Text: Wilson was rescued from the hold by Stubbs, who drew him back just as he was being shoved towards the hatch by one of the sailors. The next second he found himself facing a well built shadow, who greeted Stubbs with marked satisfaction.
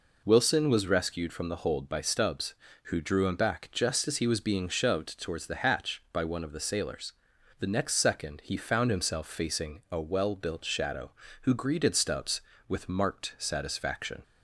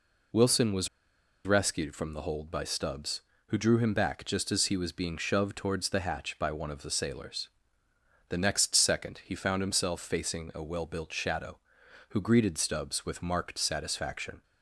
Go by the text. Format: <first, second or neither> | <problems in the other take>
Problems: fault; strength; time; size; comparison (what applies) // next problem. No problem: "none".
first | pauses between "was" and "rescued"; noticeable; at 0.8 s; 0.58 s long